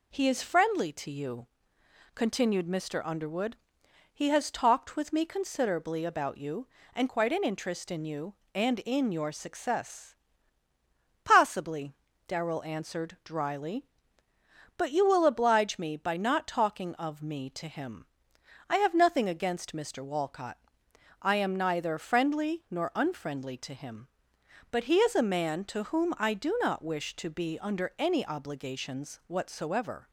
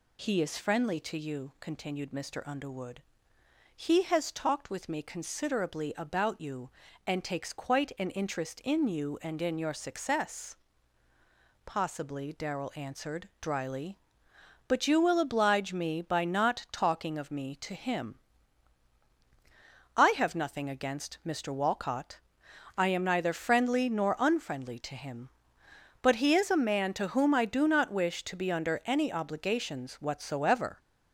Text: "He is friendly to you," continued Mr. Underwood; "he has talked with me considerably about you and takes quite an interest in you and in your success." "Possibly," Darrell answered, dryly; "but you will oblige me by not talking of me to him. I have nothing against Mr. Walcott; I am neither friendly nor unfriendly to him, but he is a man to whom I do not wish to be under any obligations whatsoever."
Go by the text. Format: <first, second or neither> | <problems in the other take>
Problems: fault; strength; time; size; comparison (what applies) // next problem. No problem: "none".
second | skips "takes"; at 7.0 s